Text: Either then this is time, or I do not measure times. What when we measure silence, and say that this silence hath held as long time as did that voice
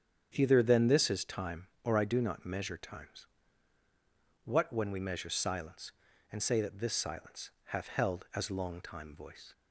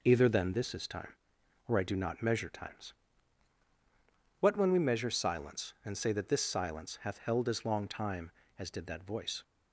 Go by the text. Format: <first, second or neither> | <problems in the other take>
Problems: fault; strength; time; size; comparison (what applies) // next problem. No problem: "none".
second | starts louder than the rest; strong; until 1.3 s; 8 dB // skips "as did that"; at 9.1 s